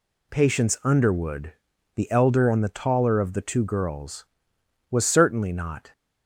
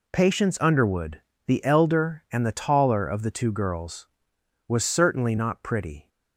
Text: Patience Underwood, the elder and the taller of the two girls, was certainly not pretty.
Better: second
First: stops before "pretty"; at 5.9 s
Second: none

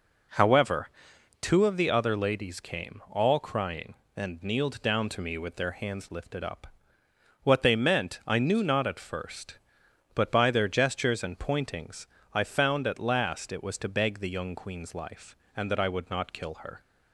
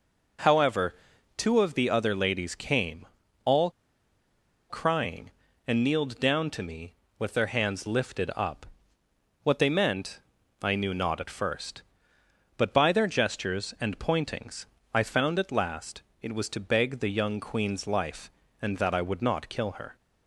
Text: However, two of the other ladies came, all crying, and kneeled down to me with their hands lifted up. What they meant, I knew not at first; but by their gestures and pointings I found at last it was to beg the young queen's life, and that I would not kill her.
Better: first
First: pauses between "pointings" and "I"; slight; at 12.0 s; 0.26 s long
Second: pauses between "all" and "crying"; at 3.6 s; 0.99 s long // pauses between "pointings" and "I"; slight; at 14.6 s; 0.30 s long // pauses between "last" and "it"; slight; at 16.0 s; 0.22 s long

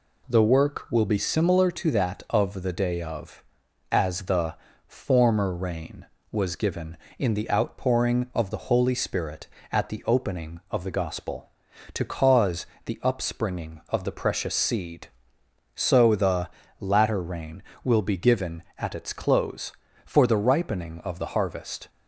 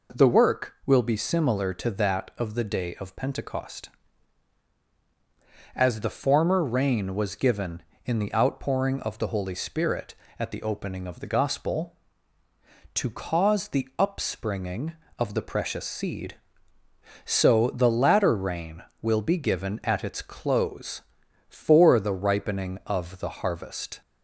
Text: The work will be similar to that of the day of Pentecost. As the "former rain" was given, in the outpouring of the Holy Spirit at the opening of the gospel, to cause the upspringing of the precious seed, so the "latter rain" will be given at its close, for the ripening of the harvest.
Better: second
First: skips "Pentecost"; at 3.6 s // pauses between "the" and "former"; slight; at 4.5 s; 0.32 s long // pauses between "cause" and "the"; slight; at 12.6 s; 0.22 s long // pauses between "the" and "latter"; slight; at 16.4 s; 0.32 s long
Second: none

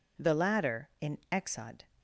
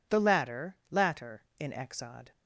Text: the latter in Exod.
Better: first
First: none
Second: says "latter" twice; at 0.8 s

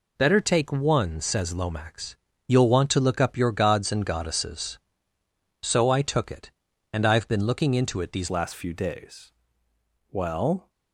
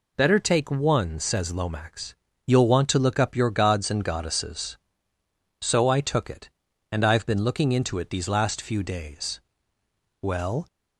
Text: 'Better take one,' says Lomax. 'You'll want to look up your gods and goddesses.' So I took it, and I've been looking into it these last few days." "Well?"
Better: second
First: changes voice at "last"; from 8.2 s on; 2.4 s long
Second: none

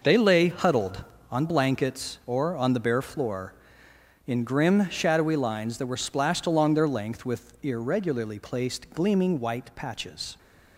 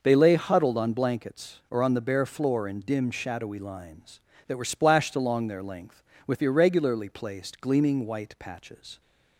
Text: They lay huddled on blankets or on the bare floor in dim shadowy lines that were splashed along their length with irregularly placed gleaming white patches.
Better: second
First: says "grim" for "dim"; at 4.4 s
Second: none

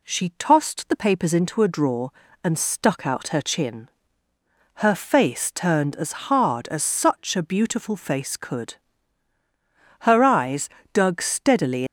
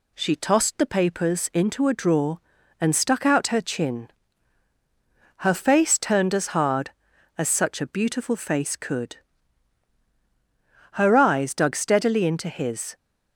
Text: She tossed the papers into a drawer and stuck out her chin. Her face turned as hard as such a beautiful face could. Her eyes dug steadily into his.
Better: second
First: pauses between "as" and "hard"; slight; at 6.1 s; 0.16 s long // pauses between "eyes" and "dug"; slight; at 10.6 s; 0.24 s long // stops before "into his"; at 11.8 s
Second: none

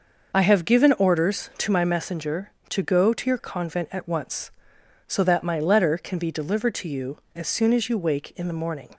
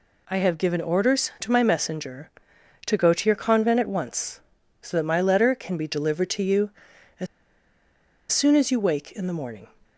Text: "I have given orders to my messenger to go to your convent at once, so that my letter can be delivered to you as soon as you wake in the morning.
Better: first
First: none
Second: pauses between "as" and "soon"; at 7.2 s; 1.0 s long

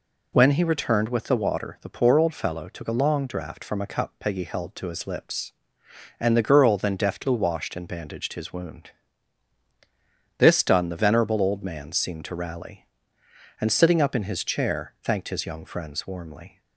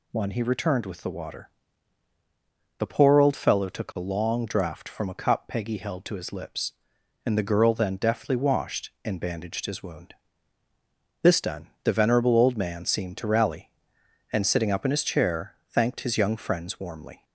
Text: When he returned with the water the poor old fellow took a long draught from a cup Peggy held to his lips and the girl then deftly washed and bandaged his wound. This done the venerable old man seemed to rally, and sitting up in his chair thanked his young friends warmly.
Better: first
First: none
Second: says "One" for "When"; at 0.1 s // pauses between "water" and "the"; strong; at 1.4 s; 1.3 s long // pauses between "chair" and "thanked"; slight; at 15.5 s; 0.16 s long

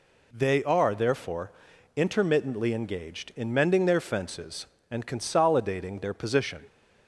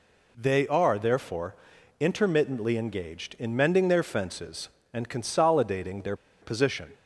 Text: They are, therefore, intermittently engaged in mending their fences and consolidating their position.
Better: first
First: none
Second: pauses between "their" and "position"; slight; at 6.1 s; 0.25 s long

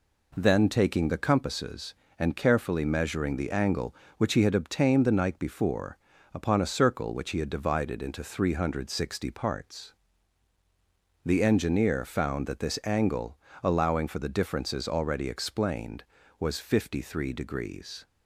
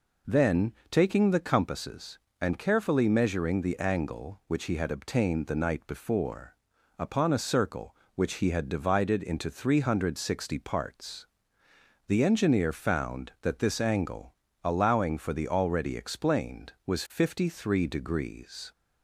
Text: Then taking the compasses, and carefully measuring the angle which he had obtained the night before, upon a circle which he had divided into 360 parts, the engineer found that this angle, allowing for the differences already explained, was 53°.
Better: first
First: none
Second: pauses between "Then" and "taking"; slight; at 0.7 s; 0.18 s long // skips "differences"; at 15.4 s

